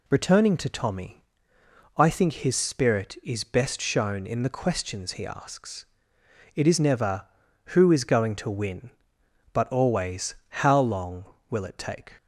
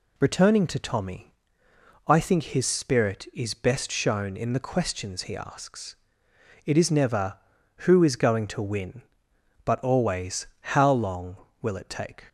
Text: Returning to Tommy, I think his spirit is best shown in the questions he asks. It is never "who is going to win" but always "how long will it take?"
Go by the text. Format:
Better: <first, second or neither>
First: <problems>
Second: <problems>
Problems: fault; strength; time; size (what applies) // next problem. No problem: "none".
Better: neither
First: none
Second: none